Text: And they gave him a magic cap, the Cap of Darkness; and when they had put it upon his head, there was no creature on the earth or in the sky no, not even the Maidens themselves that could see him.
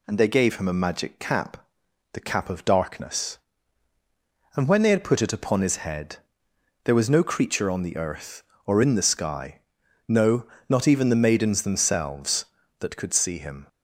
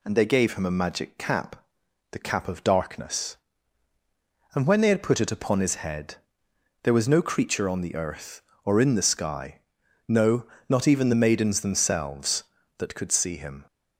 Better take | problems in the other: neither | pauses between "sky" and "no"; noticeable; the same in both

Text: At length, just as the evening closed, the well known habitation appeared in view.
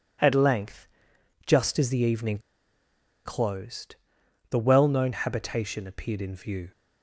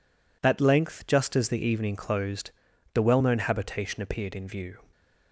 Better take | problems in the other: second | pauses between "evening" and "closed"; noticeable; at 2.3 s; 0.86 s long

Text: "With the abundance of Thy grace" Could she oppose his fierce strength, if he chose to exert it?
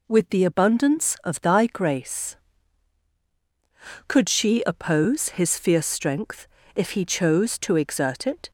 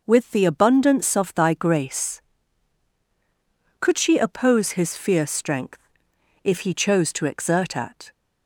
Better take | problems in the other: first | says "at" for "it"; at 7.7 s

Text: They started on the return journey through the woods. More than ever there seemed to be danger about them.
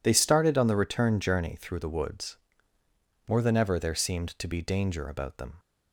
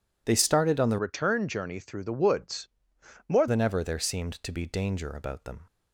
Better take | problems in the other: first | changes voice from "return" to "More"; from 0.9 to 3.4 s; 2.5 s long

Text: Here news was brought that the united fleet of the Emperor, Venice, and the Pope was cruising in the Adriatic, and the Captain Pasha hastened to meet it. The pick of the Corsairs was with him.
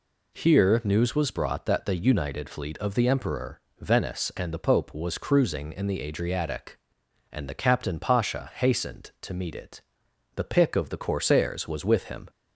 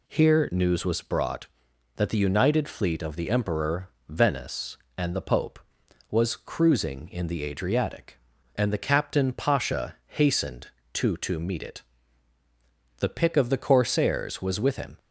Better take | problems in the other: first | says "to" twice; at 11.1 s

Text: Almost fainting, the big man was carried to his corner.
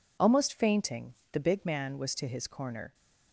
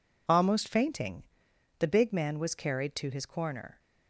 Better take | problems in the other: second | skips "carried"; at 2.1 s

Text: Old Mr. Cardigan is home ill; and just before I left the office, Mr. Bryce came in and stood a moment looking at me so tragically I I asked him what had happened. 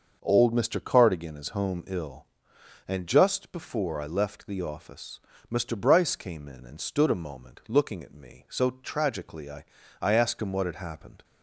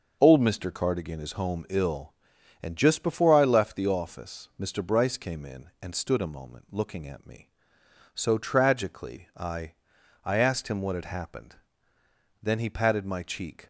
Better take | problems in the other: first | starts louder than the rest; until 1.2 s; 6.5 dB; also in the first // pauses between "I" and "I"; noticeable; at 9.7 s; 0.50 s long; also in the first // goes on to say "Then he patted my cheek"; noticeable; from 12.4 s on; 1.2 s long

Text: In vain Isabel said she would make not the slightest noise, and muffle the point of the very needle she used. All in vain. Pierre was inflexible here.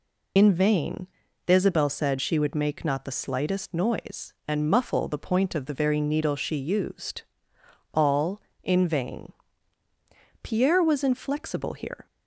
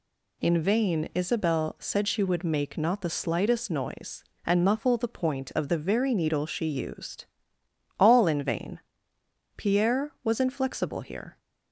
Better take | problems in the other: second | loses the start of "In"; at 0.3 s; 60 ms // pauses between "vain" and "Isabel"; at 1.0 s; 0.38 s long

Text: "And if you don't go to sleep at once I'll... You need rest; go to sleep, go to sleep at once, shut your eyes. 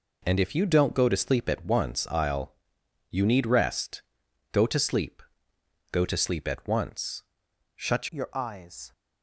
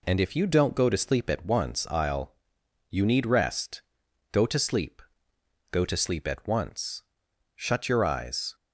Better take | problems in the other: second | changes voice at "your"; from 8.0 s on; 0.9 s long

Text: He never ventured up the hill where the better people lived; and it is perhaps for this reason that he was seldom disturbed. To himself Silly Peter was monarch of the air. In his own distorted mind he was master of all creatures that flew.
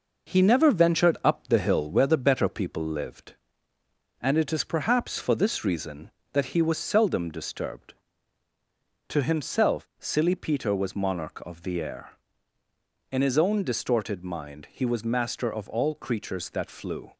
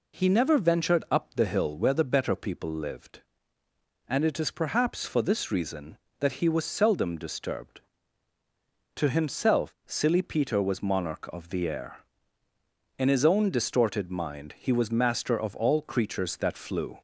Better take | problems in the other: second | gets quieter; noticeable; throughout; 5 dB

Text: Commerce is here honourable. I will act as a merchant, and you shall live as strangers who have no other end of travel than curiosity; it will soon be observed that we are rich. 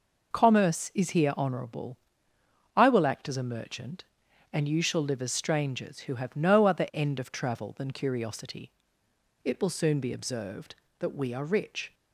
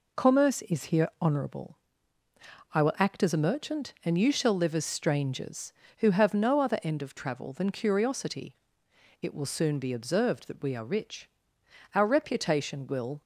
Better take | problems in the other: first | goes on to say "Our reputation will"; noticeable; from 11.9 s on; 1.2 s long

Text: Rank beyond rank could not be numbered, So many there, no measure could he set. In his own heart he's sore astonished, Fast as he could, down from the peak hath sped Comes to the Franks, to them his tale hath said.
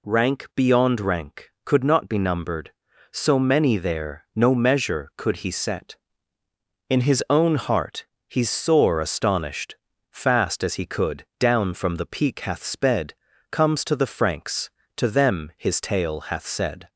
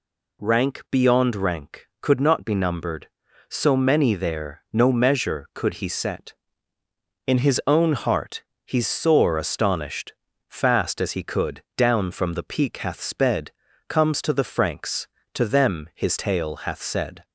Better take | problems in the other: neither | pauses between "heart" and "he's"; slight; the same in both // pauses between "sped" and "Comes"; the same in both

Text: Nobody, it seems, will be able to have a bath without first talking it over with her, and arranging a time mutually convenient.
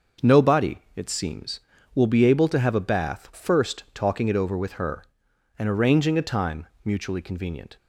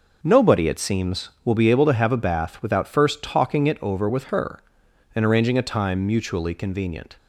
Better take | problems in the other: second | starts louder than the rest; until 1.3 s; 6 dB // skips "without"; at 3.3 s // pauses between "time" and "mutually"; slight; at 6.6 s; 0.18 s long

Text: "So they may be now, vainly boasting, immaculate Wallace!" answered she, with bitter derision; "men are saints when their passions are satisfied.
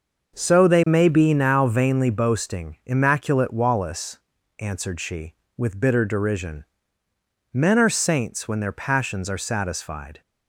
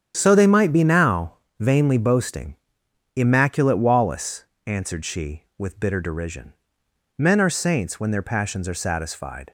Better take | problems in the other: first | starts louder than the rest; strong; until 1.1 s; 9 dB; also in the first // says "might" for "may"; at 0.4 s

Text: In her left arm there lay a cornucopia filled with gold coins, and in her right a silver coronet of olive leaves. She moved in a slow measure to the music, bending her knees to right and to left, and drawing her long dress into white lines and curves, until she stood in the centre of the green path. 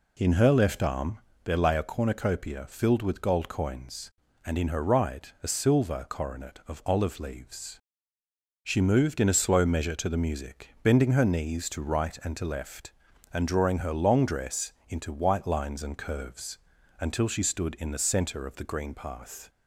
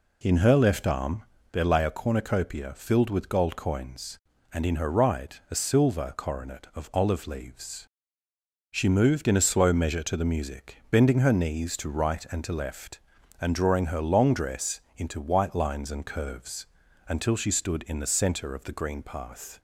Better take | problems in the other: neither | pauses between "arm" and "there"; slight; the same in both // pauses between "dress" and "into"; slight; the same in both

